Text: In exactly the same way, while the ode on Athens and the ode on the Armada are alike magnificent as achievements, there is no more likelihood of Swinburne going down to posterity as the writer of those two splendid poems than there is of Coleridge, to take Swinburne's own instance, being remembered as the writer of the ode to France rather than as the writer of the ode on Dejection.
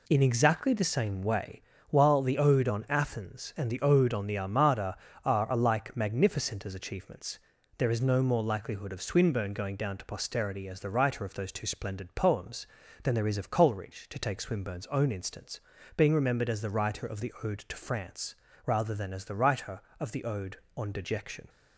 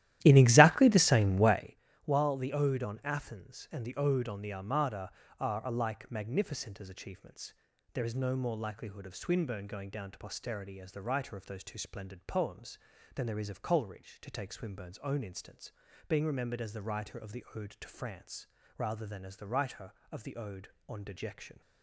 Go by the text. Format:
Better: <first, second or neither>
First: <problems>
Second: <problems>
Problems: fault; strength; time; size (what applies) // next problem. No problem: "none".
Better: first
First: pauses between "France" and "rather"; slight; at 18.3 s; 0.32 s long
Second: starts louder than the rest; strong; until 1.7 s; 14 dB // pauses between "France" and "rather"; slight; at 18.4 s; 0.32 s long